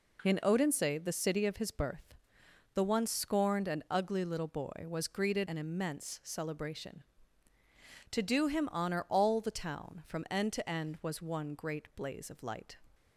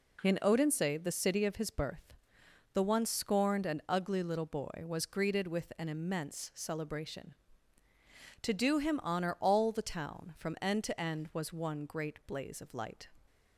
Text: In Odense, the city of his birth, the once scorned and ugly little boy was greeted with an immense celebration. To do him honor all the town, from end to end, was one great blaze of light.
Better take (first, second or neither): second